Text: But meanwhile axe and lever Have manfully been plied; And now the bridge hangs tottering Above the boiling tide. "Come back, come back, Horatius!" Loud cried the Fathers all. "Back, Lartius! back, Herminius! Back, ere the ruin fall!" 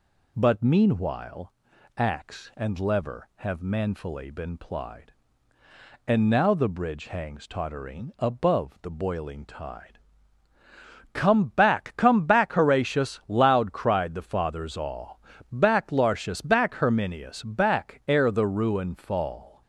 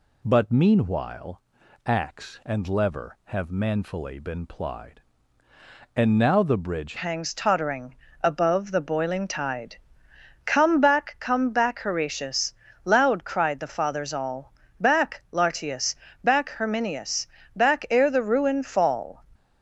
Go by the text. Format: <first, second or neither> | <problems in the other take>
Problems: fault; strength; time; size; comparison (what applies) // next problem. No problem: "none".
first | pauses between "meanwhile" and "axe"; at 1.4 s; 0.44 s long; also in the first // changes voice at "hangs"; from 6.9 s on; 12.3 s long // pauses between "tottering" and "Above"; slight; at 7.9 s; 0.28 s long